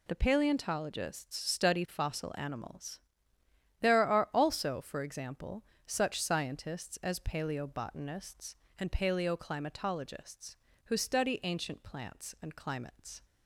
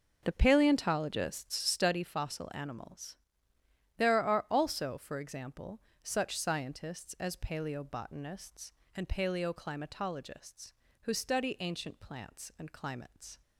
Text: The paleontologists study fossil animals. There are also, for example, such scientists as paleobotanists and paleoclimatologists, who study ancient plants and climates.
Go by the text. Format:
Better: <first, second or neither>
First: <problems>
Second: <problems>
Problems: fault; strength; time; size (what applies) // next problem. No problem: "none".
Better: first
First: none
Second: starts louder than the rest; noticeable; until 1.9 s; 6 dB